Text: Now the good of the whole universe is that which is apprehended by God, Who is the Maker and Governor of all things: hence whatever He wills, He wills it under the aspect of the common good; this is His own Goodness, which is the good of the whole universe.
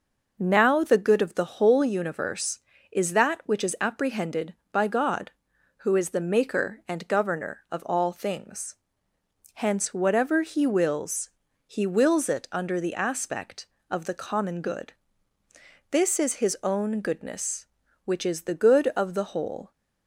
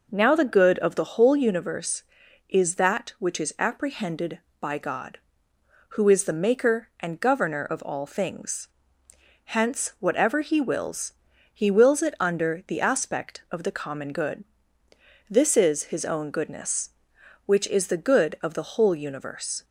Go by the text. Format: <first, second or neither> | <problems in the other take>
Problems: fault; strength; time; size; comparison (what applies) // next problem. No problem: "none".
second | stops before "universe"; at 19.7 s